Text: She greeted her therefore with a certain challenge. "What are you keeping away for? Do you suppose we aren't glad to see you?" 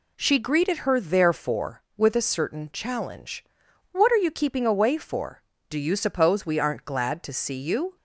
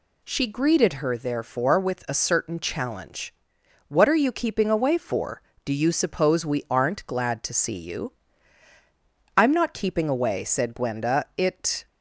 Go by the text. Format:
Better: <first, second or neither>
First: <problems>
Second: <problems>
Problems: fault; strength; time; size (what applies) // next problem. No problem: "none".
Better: first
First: none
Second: goes on to say "I'm not keeping away said Gwenda It"; strong; from 9.3 s on; 2.5 s long